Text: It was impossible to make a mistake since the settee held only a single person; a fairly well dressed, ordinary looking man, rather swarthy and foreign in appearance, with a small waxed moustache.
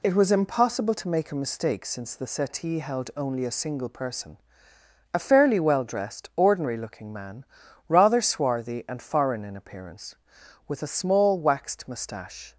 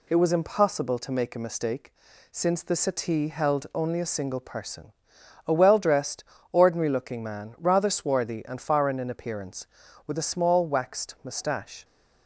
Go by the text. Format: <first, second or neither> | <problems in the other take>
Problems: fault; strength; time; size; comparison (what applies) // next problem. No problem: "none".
first | pauses between "mistake" and "since"; at 1.9 s; 0.38 s long // skips "fairly"; at 5.5 s